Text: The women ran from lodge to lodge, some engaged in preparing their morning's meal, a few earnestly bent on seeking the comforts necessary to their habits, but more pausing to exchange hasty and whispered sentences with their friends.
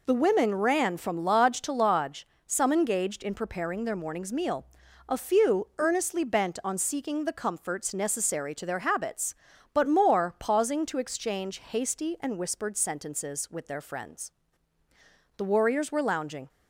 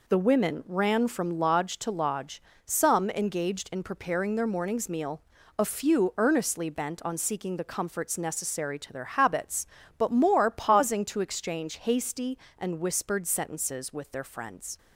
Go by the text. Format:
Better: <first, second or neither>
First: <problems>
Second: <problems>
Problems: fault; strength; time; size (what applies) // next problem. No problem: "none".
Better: second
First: goes on to say "The warriors were lounging"; noticeable; from 15.3 s on; 1.1 s long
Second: none